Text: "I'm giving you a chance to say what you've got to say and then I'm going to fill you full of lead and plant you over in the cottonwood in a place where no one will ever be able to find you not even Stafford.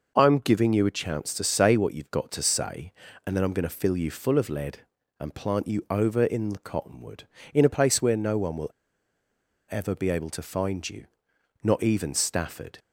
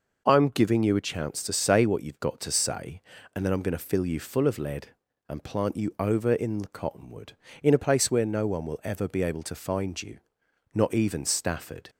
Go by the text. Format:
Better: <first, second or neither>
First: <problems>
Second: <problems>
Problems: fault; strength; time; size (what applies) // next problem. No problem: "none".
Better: second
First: pauses between "will" and "ever"; at 8.7 s; 1.0 s long // pauses between "you" and "not"; noticeable; at 11.0 s; 0.56 s long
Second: pauses between "you" and "not"; noticeable; at 10.1 s; 0.54 s long